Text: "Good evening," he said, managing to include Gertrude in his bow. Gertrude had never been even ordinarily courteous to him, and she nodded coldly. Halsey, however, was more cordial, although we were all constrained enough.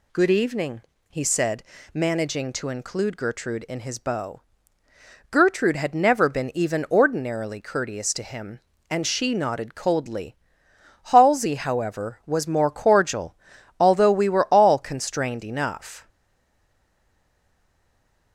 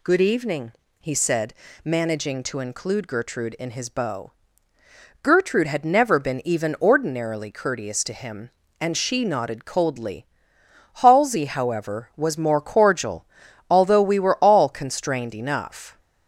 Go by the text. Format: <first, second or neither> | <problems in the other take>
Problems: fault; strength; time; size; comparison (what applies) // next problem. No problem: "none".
second | stays silent after the last word; from 16.0 s on; 2.3 s long